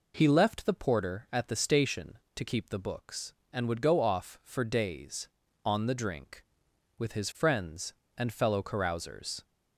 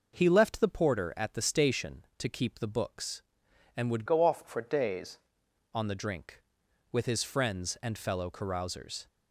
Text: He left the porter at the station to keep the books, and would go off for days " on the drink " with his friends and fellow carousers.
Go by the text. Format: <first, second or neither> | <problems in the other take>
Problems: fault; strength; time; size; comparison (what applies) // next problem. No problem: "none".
first | starts louder than the rest; noticeable; until 1.2 s; 6 dB // changes voice from "go" to "days"; from 4.0 to 5.1 s; 1.1 s long